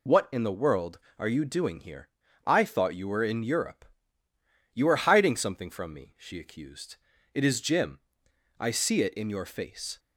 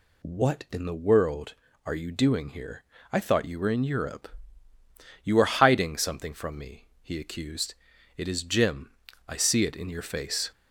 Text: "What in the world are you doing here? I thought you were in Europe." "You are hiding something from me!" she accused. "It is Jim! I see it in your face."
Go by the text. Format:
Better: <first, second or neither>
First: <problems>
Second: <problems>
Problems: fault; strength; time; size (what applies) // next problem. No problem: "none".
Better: first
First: none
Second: says "he" for "she"; at 7.0 s